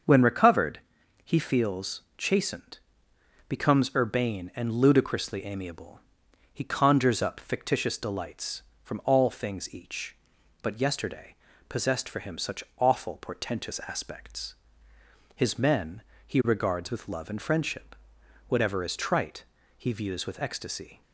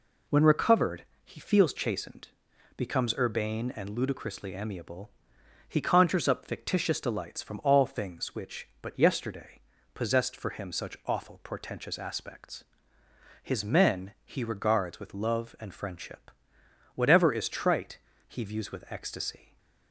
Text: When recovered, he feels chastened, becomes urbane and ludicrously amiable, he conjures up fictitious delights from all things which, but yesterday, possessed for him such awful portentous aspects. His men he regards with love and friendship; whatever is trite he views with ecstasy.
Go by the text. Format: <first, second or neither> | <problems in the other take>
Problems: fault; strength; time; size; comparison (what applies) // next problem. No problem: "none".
second | starts louder than the rest; until 1.5 s; 6.5 dB // pauses between "feels" and "chastened"; slight; at 2.0 s; 0.16 s long // says "each" for "which"; at 9.7 s // pauses between "men" and "he"; slight; at 16.0 s; 0.24 s long // pauses between "trite" and "he"; slight; at 19.4 s; 0.34 s long; slight in the second